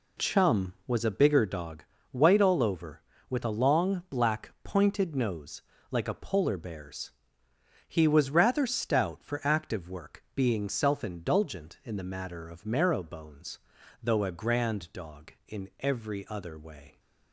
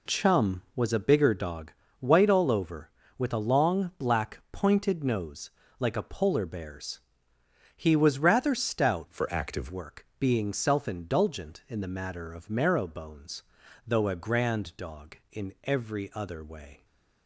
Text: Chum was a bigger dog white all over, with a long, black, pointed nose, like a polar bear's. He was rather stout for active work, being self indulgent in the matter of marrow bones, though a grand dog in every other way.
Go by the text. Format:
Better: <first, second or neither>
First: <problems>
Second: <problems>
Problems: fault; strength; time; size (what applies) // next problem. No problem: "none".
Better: first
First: pauses between "dog" and "white"; slight; at 1.8 s; 0.26 s long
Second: pauses between "dog" and "white"; slight; at 1.7 s; 0.26 s long // changes voice from "for" to "active"; from 9.0 to 9.7 s; 0.7 s long